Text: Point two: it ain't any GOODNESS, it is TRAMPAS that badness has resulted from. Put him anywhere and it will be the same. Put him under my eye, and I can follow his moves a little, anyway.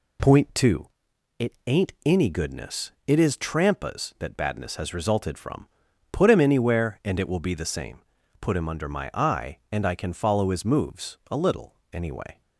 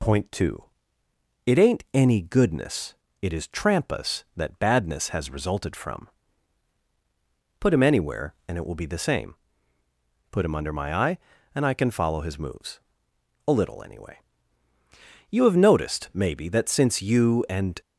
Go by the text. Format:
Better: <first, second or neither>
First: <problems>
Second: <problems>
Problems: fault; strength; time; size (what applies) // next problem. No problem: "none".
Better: first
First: none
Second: pauses between "moves" and "a"; noticeable; at 12.8 s; 0.66 s long // goes on to say "You have noticed maybe that since you and"; strong; from 15.3 s on; 2.5 s long